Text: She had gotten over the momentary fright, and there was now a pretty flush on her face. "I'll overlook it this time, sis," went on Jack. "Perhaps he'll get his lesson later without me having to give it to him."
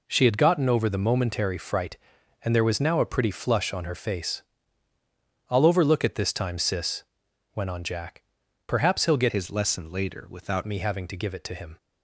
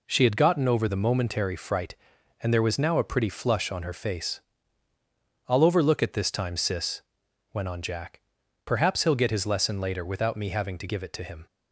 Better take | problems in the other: second | changes voice from "his" to "without"; from 9.2 to 10.6 s; 1.4 s long

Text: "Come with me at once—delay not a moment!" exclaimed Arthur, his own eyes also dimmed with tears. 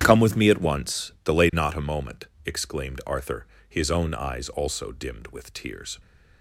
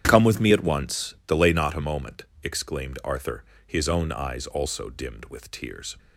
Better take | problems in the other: neither | starts louder than the rest; strong; the same in both

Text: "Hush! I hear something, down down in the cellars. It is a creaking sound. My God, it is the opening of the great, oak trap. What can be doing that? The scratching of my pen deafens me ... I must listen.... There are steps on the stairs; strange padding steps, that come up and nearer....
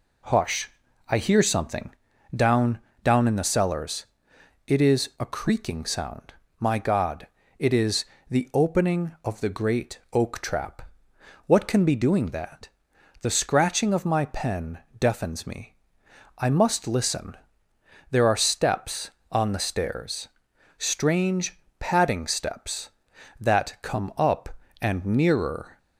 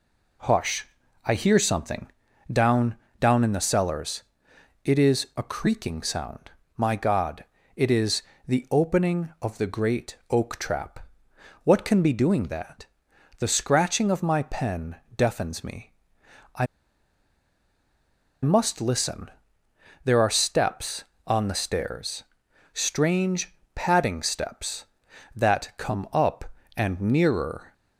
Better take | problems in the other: first | pauses between "down" and "down"; slight; at 2.9 s; 0.24 s long; slight in the first // pauses between "is" and "the"; slight; at 8.2 s; 0.24 s long; slight in the first // pauses between "pen" and "deafens"; slight; at 14.9 s; 0.20 s long; slight in the first // pauses between "I" and "must"; strong; at 16.6 s; 1.7 s long // pauses between "strange" and "padding"; slight; at 23.5 s; 0.18 s long; slight in the first

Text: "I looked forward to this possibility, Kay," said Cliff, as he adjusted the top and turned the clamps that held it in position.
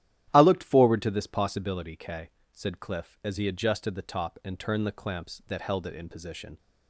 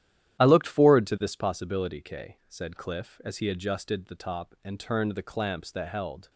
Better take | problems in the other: first | starts louder than the rest; strong; until 1.4 s; 11.5 dB; strong in the first // stops before "it in position"; at 6.2 s

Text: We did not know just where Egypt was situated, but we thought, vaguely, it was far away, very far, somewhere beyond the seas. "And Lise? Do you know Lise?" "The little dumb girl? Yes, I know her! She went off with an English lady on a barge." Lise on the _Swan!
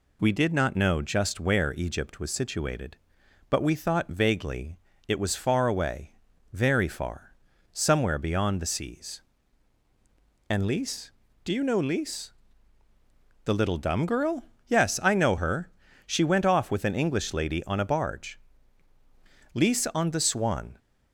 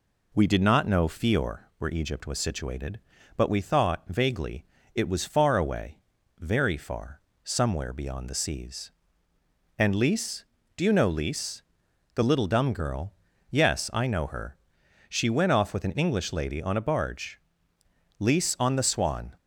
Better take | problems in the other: first | says "fior" for "just"; at 1.0 s

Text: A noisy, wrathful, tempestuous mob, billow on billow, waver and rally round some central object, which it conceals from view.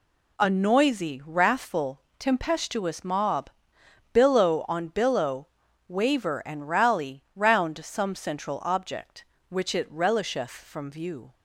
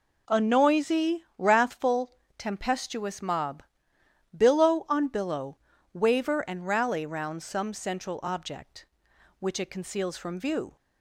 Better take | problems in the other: second | says "relisheth" for "conceals"; at 9.9 s

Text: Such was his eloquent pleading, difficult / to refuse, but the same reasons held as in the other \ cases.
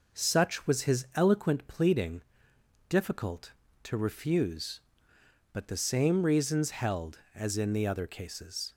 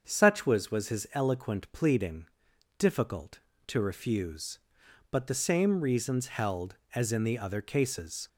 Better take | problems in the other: first | starts louder than the rest; until 1.0 s; 7 dB // says "was" twice; at 0.6 s

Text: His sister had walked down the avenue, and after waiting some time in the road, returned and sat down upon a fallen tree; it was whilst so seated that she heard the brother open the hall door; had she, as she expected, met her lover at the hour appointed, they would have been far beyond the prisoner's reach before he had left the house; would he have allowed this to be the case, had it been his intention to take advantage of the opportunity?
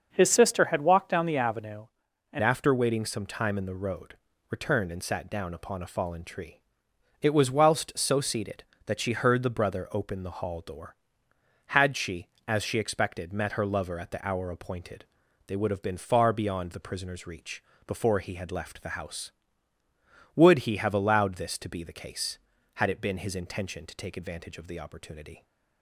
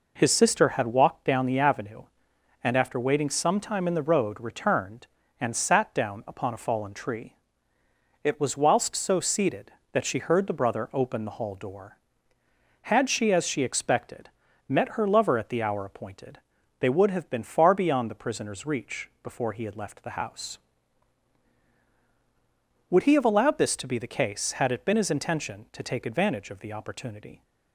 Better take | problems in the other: second | starts louder than the rest; until 1.1 s; 6.5 dB // changes voice at "after"; from 2.4 s on; 23.0 s long // pauses between "reach" and "before"; slight; at 17.6 s; 0.24 s long

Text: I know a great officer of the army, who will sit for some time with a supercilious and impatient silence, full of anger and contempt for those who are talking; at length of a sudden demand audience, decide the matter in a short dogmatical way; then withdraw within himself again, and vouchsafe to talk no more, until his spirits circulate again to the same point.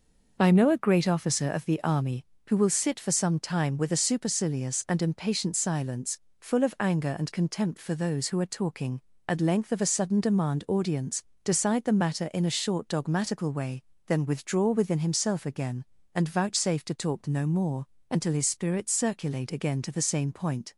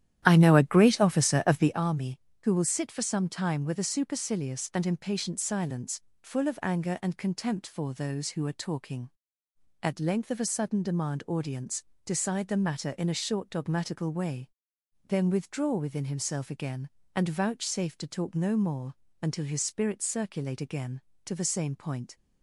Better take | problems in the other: first | starts louder than the rest; strong; until 1.8 s; 12 dB

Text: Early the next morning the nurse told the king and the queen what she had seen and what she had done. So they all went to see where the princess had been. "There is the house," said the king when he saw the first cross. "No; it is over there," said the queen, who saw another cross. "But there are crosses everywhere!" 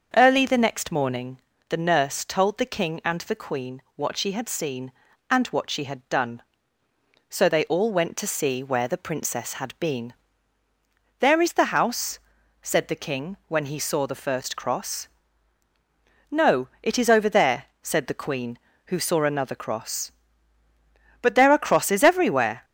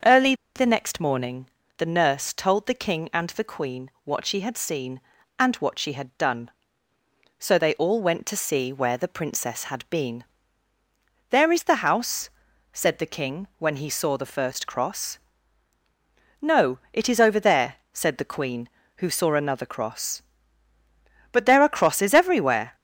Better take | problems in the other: first | starts louder than the rest; until 1.2 s; 6.5 dB; also in the first // pauses between "Early" and "the"; slight; at 0.3 s; 0.22 s long // pauses between "morning" and "the"; slight; at 1.4 s; 0.32 s long; slight in the first // pauses between "queen" and "what"; slight; at 3.8 s; 0.16 s long; slight in the first

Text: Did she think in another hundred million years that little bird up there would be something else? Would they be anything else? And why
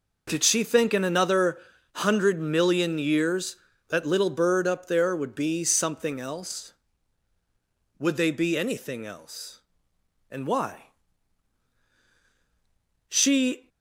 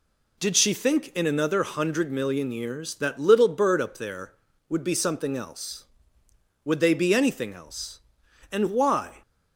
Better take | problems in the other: second | pauses between "another" and "hundred"; slight; at 1.5 s; 0.36 s long // goes on to say "She"; from 13.0 s on; 0.60 s long

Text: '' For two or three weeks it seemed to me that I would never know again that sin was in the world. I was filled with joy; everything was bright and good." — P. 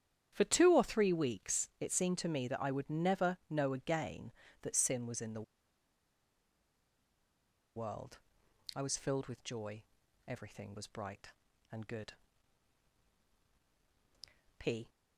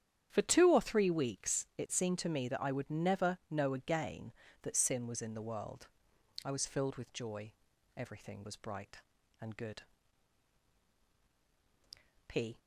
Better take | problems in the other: second | starts louder than the rest; strong; until 1.3 s; 9.5 dB; strong in the second // pauses between "the" and "world"; strong; at 5.4 s; 2.3 s long

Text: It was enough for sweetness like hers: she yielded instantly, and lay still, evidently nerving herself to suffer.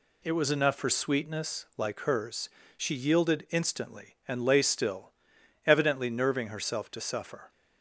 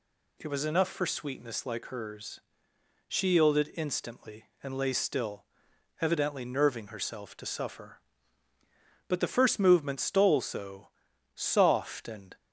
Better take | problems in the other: first | goes on to say "But the first movement stole so soft and"; strong; from 9.0 s on; 3.2 s long

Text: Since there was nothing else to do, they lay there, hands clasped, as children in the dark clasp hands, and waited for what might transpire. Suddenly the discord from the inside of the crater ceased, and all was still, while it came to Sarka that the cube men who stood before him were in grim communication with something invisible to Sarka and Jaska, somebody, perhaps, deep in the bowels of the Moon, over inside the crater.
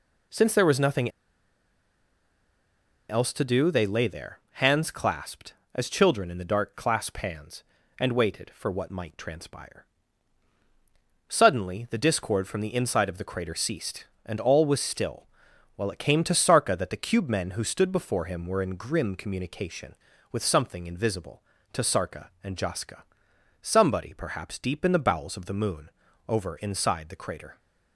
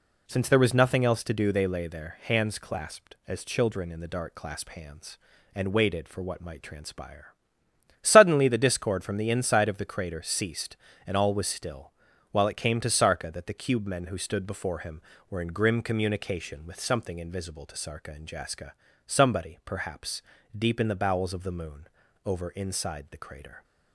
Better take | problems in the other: second | pauses between "nothing" and "else"; strong; at 1.0 s; 1.9 s long

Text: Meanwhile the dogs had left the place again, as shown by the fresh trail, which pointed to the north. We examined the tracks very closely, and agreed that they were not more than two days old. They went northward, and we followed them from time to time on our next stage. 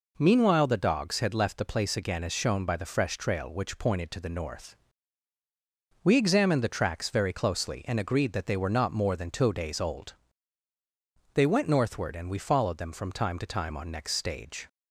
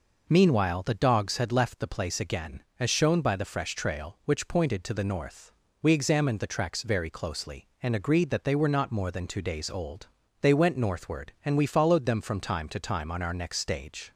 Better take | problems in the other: second | skips "our"; at 13.8 s

